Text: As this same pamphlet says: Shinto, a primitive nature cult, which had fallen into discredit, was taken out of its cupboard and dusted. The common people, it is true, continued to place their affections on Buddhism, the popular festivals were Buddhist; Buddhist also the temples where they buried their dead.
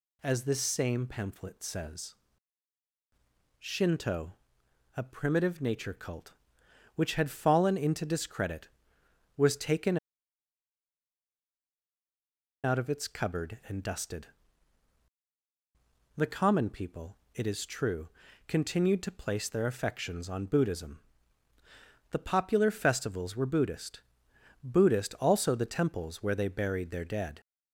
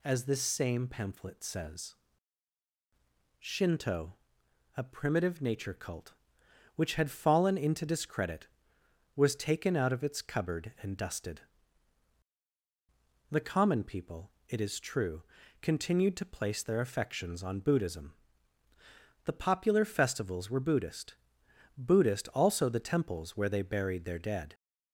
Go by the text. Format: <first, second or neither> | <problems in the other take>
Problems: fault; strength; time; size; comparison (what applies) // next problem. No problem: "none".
second | pauses between "taken" and "out"; strong; at 9.9 s; 2.6 s long